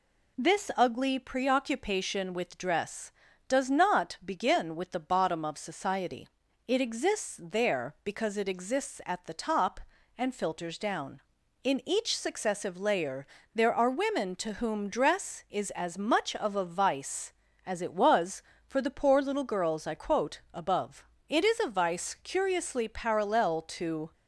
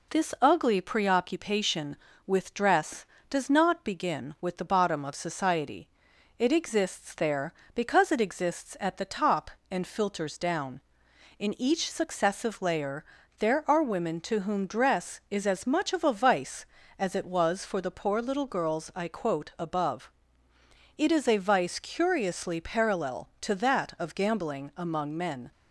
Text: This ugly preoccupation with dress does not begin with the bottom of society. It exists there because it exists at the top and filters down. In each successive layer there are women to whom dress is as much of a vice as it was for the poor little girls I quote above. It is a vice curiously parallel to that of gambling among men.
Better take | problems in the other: second | pauses between "layer" and "there"; slight; at 13.2 s; 0.26 s long; slight in the second // stops before "that of gambling among men"; at 24.1 s

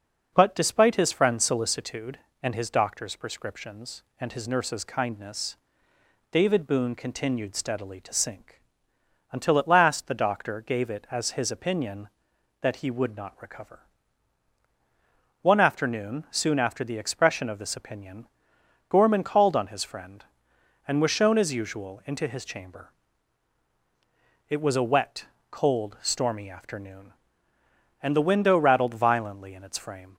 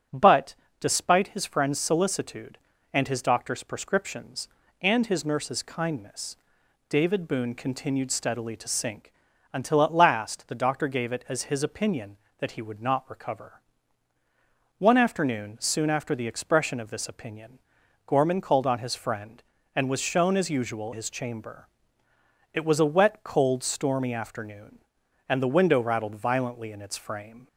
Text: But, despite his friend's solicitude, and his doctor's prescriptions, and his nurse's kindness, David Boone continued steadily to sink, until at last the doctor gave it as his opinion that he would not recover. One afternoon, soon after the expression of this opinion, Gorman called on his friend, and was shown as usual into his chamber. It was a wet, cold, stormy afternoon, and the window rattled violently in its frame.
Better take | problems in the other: first | starts louder than the rest; strong; until 1.3 s; 8.5 dB // skips "into"; at 20.9 s

